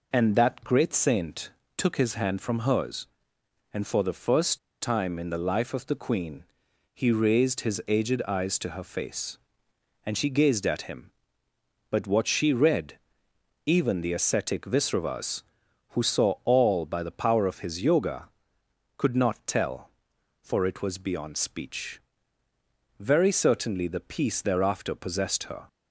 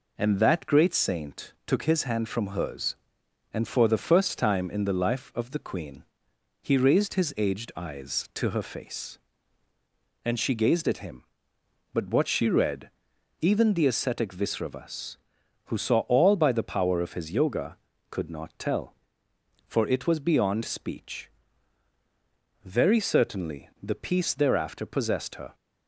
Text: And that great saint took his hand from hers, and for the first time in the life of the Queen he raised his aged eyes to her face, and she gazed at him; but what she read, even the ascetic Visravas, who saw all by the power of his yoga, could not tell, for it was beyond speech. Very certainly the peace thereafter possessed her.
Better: second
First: pauses between "saint" and "took"; slight; at 1.5 s; 0.26 s long // pauses between "first" and "time"; slight; at 4.5 s; 0.22 s long // pauses between "Queen" and "he"; noticeable; at 6.4 s; 0.48 s long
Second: pauses between "Queen" and "he"; noticeable; at 6.0 s; 0.58 s long

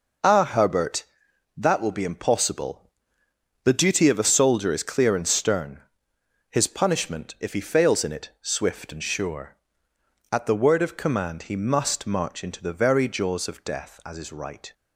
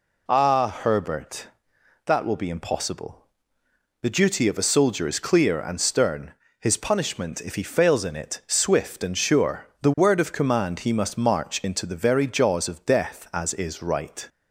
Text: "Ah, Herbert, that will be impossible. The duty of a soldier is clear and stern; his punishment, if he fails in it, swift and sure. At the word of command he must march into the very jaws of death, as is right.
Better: first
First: none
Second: skips "At"; at 9.7 s

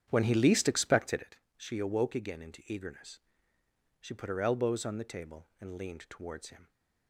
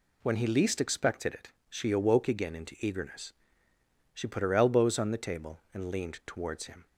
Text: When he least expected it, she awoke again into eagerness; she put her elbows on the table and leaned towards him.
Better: second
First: starts louder than the rest; strong; until 1.3 s; 9 dB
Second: none

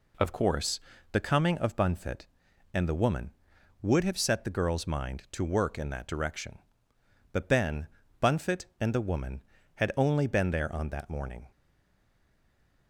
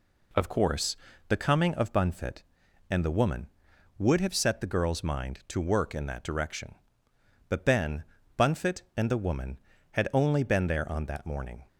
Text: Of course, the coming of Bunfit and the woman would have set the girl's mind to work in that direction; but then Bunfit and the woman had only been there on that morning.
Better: second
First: pauses between "then" and "Bunfit"; slight; at 7.8 s; 0.34 s long // stays silent after the last word; noticeable; from 11.5 s on; 1.3 s long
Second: pauses between "then" and "Bunfit"; slight; at 8.0 s; 0.34 s long

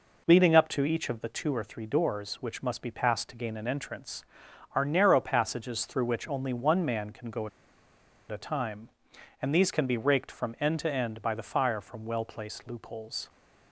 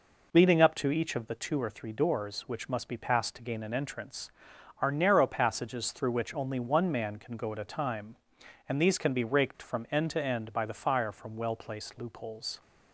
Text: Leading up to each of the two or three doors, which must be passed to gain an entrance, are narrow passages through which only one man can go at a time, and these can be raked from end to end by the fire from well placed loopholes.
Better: second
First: pauses between "at" and "a"; noticeable; at 7.4 s; 0.81 s long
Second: none

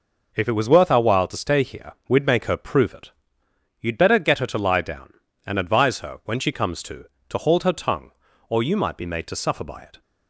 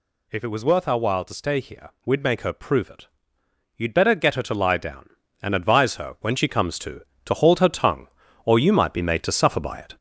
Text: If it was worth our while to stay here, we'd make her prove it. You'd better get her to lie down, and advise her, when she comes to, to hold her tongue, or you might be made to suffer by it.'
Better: first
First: none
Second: gets louder; noticeable; throughout; 4 dB

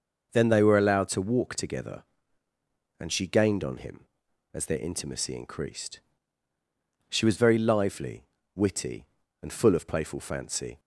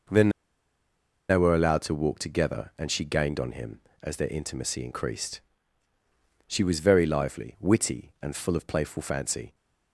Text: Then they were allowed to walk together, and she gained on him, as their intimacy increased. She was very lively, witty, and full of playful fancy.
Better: first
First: none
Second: pauses between "Then" and "they"; at 0.2 s; 1.0 s long

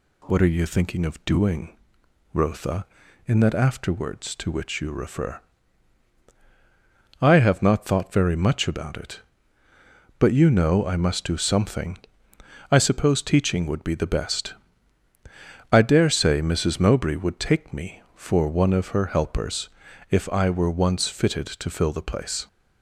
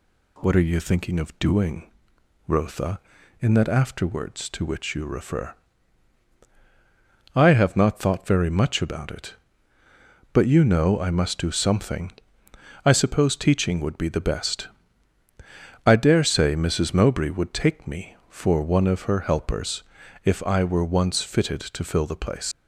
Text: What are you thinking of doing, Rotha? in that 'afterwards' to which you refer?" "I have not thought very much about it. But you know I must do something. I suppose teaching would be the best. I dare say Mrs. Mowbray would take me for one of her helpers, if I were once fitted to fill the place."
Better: first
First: none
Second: leaves "place" unfinished; at 22.5 s; 95 ms

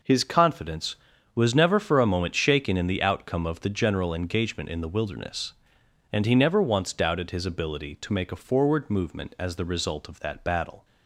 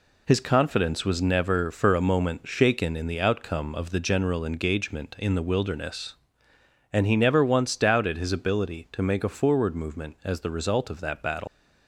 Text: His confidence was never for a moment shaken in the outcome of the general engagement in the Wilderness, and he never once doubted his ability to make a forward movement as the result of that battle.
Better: first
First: none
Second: leaves "battle" unfinished; at 11.4 s; 135 ms

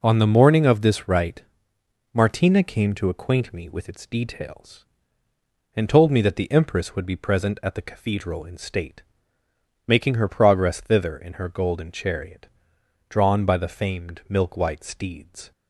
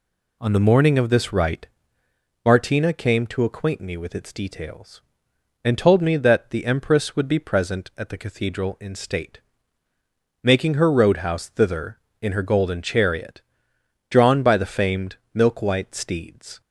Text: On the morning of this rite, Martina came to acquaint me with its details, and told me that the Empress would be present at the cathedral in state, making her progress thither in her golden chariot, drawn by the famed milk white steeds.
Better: first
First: none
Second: says "roadhouse" for "progress"; at 10.9 s // pauses between "famed" and "milk"; slight; at 15.1 s; 0.18 s long

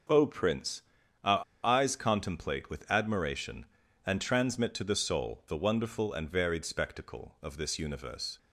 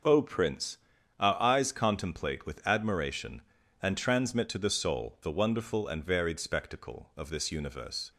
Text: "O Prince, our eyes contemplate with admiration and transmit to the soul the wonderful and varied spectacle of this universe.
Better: second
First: starts louder than the rest; until 1.7 s; 6.5 dB // pauses between "our" and "eyes"; slight; at 1.4 s; 0.21 s long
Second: starts louder than the rest; until 1.4 s; 6 dB

